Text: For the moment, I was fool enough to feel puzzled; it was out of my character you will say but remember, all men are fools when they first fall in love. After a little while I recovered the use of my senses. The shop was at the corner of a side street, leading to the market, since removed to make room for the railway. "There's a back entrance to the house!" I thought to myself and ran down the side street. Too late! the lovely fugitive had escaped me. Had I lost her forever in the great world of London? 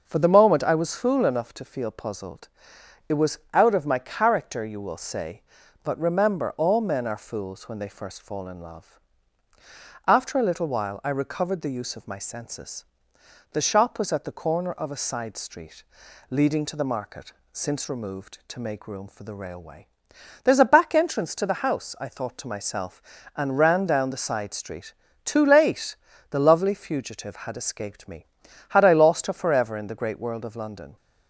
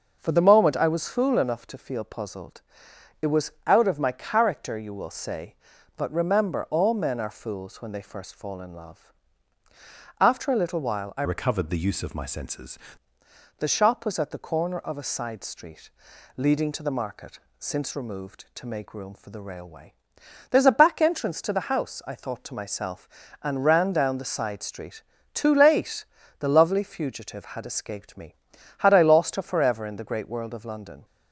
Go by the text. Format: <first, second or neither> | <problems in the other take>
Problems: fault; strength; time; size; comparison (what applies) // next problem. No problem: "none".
first | starts louder than the rest; until 1.2 s; 6.5 dB; also in the first // changes voice from "recovered" to "senses"; from 11.2 to 12.7 s; 1.5 s long